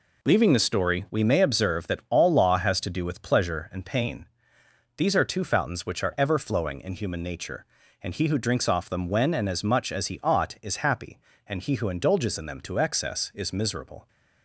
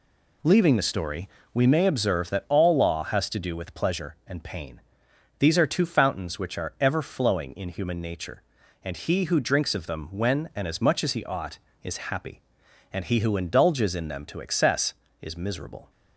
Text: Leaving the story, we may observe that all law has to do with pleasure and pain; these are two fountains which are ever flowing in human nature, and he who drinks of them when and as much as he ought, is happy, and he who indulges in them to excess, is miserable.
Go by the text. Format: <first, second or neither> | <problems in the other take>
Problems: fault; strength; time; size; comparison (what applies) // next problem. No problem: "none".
second | says "off" for "of"; at 8.6 s